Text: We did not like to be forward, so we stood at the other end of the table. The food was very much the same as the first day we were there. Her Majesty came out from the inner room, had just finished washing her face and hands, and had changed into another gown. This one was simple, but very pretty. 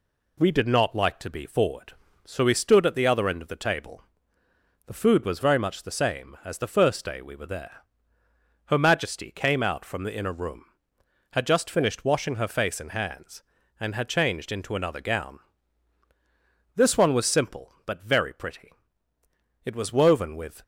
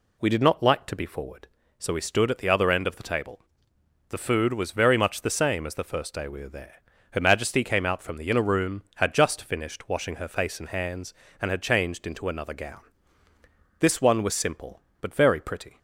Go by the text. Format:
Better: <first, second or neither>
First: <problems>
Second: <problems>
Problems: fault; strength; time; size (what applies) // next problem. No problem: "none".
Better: second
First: goes on to say "It was woven with"; noticeable; from 19.6 s on; 0.98 s long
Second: none